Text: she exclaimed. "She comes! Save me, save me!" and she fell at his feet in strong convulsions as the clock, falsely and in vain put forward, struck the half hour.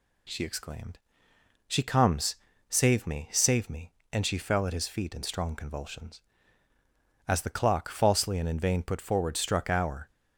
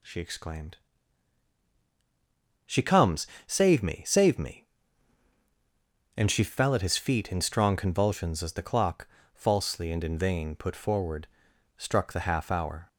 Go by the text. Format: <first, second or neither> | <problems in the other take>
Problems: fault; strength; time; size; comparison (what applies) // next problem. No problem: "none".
second | skips "the half"; at 9.6 s